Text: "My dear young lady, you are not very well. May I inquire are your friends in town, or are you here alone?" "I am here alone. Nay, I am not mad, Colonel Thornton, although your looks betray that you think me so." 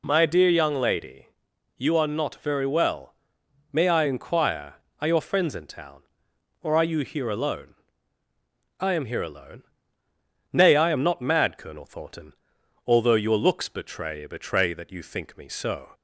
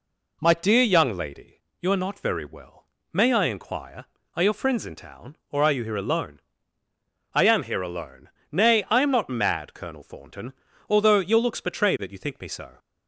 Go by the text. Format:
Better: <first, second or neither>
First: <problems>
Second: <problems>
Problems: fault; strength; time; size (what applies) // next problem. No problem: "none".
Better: second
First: says "betray" twice; at 14.2 s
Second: none